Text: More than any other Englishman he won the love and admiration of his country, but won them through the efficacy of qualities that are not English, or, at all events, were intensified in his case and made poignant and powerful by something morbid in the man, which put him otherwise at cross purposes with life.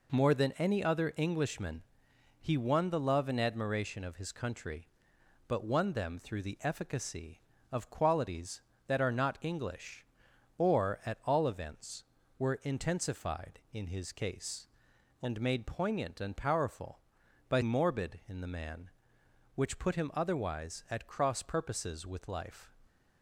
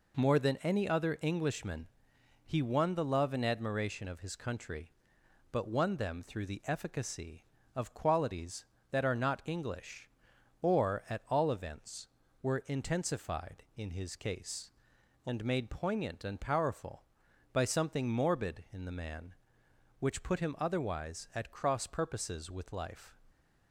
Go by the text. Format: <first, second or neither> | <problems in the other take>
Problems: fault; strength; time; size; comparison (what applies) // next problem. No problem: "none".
second | pauses between "Englishman" and "he"; noticeable; at 1.8 s; 0.60 s long; noticeable in the second // skips "something"; at 17.6 s